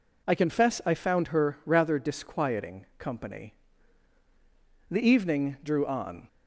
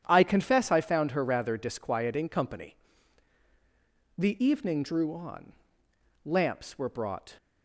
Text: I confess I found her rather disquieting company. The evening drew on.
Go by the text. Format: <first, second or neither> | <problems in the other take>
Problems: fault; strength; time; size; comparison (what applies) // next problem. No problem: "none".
first | starts louder than the rest; strong; until 1.0 s; 9.5 dB // goes on to say "Lamps were brought"; noticeable; from 6.2 s on; 1.1 s long